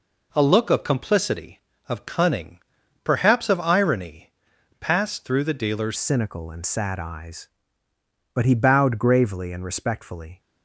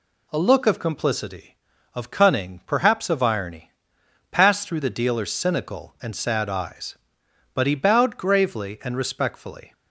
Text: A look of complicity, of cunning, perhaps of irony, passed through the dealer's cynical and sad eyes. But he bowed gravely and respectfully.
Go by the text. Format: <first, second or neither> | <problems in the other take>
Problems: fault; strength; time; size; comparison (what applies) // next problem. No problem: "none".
second | changes voice at "cynical"; from 5.9 s on; 4.4 s long